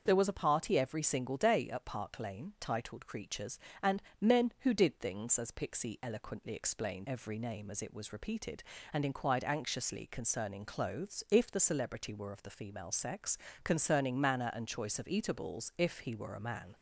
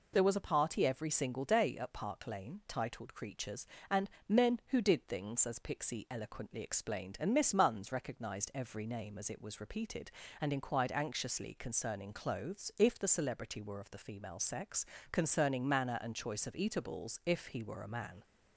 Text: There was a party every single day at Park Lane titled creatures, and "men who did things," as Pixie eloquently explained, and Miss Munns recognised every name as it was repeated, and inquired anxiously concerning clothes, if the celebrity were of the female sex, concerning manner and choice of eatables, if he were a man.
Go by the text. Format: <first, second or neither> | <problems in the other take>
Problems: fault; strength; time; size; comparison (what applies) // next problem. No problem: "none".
second | starts louder than the rest; until 1.0 s; 6.5 dB // pauses between "and" and "men"; slight; at 4.0 s; 0.20 s long; slight in the second // skips "and Miss Munns recognised"; at 7.0 s